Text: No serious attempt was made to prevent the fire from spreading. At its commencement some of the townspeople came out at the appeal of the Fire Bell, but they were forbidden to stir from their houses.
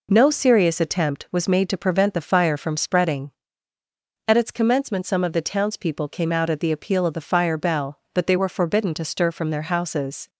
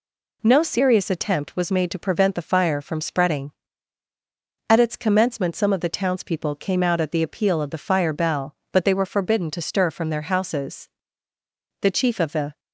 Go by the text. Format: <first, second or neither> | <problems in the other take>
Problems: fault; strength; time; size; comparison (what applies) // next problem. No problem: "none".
first | goes on to say "The Chief of the"; noticeable; from 11.8 s on; 0.78 s long